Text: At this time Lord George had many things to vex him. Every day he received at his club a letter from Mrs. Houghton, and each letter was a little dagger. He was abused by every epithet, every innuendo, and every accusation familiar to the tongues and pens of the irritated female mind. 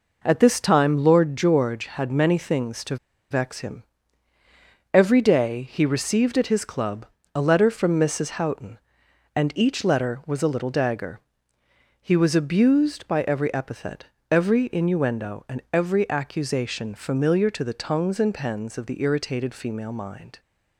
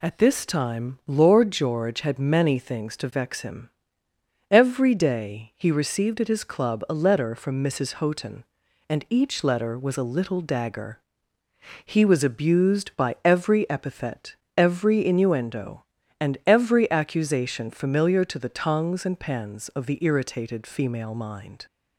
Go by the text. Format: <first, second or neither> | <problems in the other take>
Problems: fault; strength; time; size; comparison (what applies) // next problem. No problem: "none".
second | pauses between "to" and "vex"; slight; at 2.9 s; 0.35 s long // pauses between "club" and "a"; slight; at 7.0 s; 0.28 s long